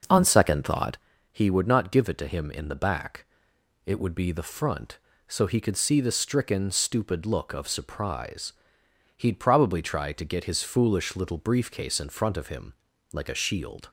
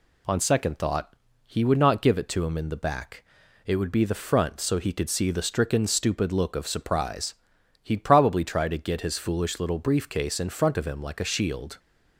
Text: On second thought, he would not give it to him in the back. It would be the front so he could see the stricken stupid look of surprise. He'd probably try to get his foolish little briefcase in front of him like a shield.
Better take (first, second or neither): second